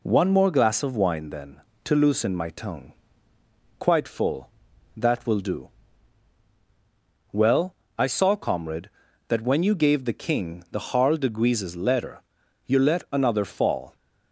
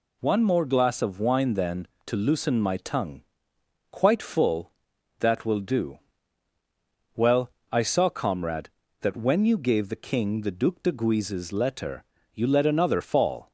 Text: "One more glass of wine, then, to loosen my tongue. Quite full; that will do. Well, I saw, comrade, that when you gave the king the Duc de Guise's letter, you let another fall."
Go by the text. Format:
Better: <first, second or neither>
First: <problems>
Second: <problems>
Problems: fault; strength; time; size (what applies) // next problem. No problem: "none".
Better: second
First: says "Harl" for "Duc"; at 10.9 s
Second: none